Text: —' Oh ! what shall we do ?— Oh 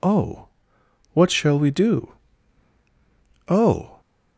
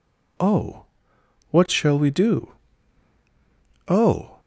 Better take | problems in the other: neither | none

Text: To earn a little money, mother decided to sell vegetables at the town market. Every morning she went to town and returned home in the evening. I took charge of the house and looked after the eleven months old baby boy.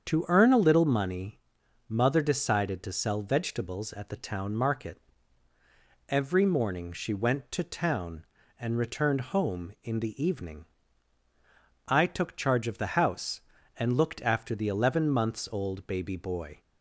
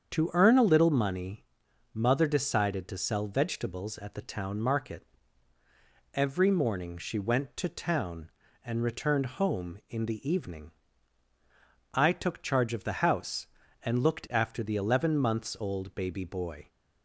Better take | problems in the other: neither | starts louder than the rest; strong; the same in both

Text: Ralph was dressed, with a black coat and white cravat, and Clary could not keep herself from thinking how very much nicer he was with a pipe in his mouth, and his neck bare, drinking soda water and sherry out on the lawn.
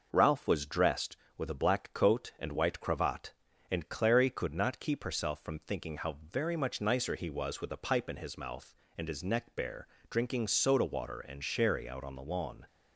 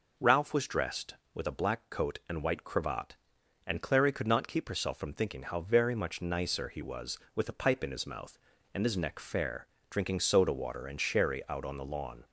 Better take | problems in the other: first | says "fair" for "bare"; at 9.1 s

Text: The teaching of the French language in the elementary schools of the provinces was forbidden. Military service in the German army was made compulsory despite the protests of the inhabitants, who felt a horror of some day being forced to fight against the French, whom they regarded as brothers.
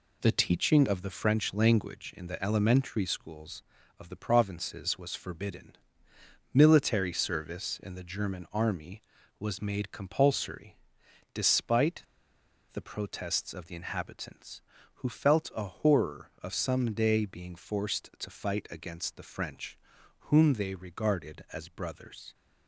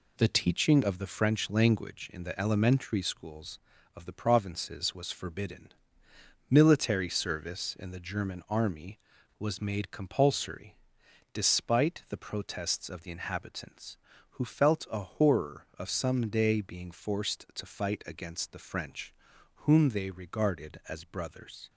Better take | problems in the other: second | pauses between "compulsory" and "despite"; noticeable; at 10.7 s; 0.56 s long; noticeable in the second // pauses between "despite" and "the"; noticeable; at 12.0 s; 0.71 s long

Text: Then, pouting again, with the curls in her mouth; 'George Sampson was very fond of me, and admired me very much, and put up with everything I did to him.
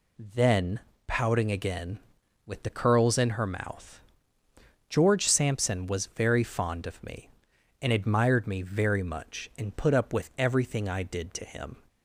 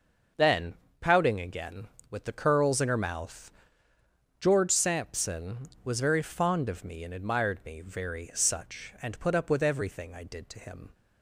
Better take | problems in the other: first | says "such" for "much"; at 8.3 s

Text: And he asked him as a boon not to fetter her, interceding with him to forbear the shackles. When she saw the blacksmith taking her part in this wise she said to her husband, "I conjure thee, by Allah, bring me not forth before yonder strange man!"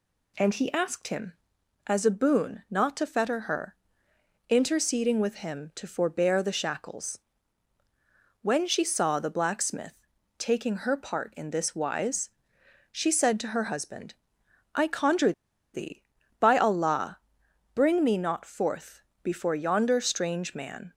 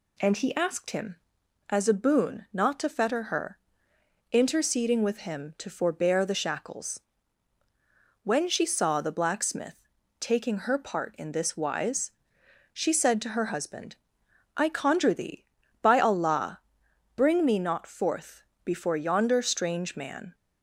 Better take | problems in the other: second | pauses between "blacksmith" and "taking"; at 9.9 s; 0.44 s long; also in the second // pauses between "wise" and "she"; noticeable; at 12.2 s; 0.66 s long; noticeable in the second // pauses between "conjure" and "thee"; at 15.3 s; 0.41 s long // pauses between "forth" and "before"; slight; at 19.0 s; 0.22 s long; slight in the second

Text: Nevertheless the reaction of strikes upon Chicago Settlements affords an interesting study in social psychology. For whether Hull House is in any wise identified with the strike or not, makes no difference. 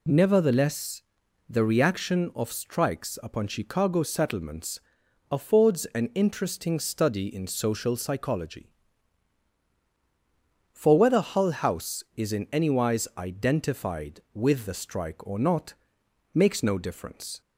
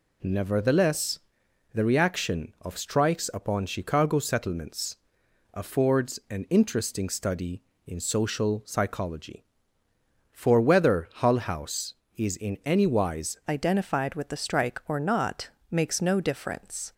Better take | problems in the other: first | pauses between "Nevertheless" and "the"; noticeable; at 1.1 s; 0.54 s long; noticeable in the first // pauses between "Settlements" and "affords"; noticeable; at 4.9 s; 0.56 s long; noticeable in the first // changes voice at "identified"; from 13.4 s on; 3.5 s long

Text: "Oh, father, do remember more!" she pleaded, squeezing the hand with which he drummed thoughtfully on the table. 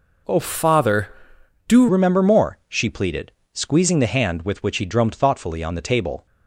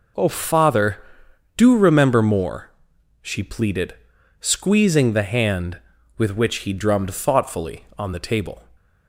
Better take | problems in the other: second | changes voice at "remember"; from 1.8 s on; 4.4 s long

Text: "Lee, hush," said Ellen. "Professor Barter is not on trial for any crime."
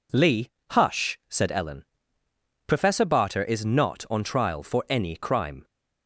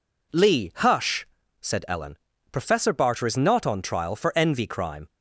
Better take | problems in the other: first | says "envy" for "any"; at 4.3 s

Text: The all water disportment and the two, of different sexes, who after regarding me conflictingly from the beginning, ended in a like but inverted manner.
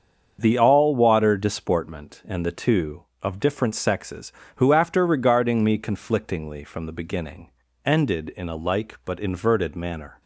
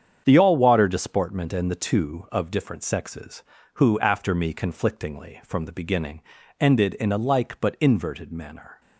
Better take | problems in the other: first | starts louder than the rest; strong; until 1.2 s; 7.5 dB; also in the first // skips "regarding"; at 4.3 s

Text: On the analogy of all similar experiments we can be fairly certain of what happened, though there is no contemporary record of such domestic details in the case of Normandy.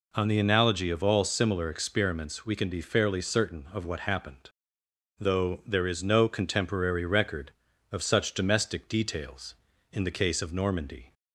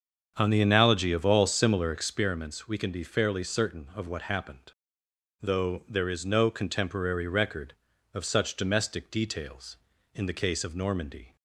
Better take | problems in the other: first | starts louder than the rest; until 2.3 s; 7 dB

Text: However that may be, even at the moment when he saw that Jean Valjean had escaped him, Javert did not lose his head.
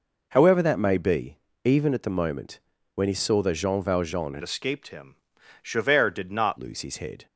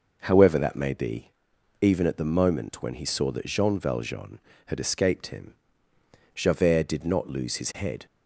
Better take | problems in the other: second | pauses between "moment" and "when"; slight; at 2.5 s; 0.34 s long // changes voice from "escaped" to "not"; from 4.4 to 6.5 s; 2.1 s long

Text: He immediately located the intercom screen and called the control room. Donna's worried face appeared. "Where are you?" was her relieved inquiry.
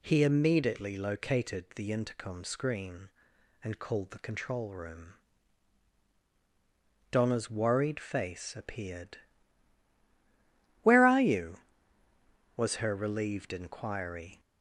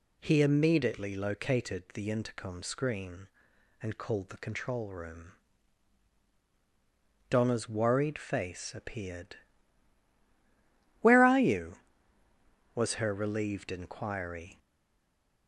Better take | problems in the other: first | stays silent after the last word; slight; from 14.5 s on; 0.9 s long

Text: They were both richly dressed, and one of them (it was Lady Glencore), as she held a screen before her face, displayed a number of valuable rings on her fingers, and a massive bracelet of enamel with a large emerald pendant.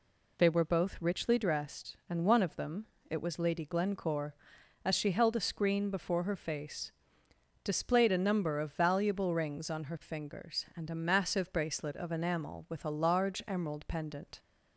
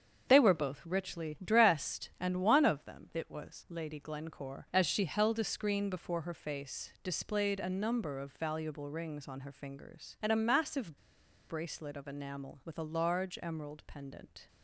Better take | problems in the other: first | starts louder than the rest; strong; until 1.2 s; 7 dB // pauses between "massive" and "bracelet"; noticeable; at 10.9 s; 0.51 s long

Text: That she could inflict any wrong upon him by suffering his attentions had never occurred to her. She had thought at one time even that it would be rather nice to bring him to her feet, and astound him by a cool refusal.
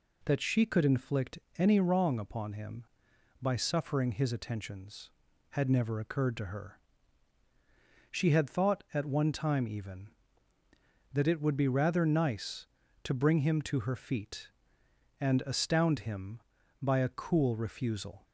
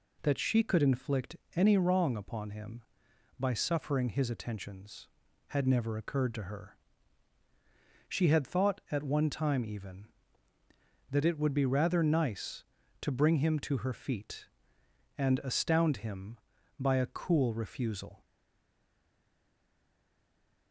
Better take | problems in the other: first | pauses between "inflict" and "any"; slight; at 1.3 s; 0.20 s long; slight in the first // stays silent after the last word; from 18.2 s on; 2.5 s long

